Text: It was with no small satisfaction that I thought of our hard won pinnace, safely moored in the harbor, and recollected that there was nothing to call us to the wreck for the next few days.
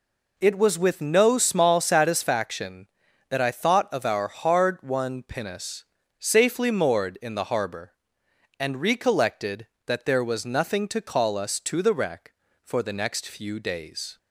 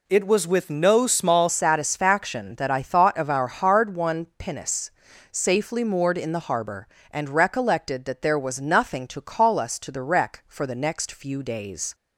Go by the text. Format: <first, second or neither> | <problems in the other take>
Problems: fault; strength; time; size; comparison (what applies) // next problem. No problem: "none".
first | changes voice at "satisfaction"; from 1.4 s on; 10.5 s long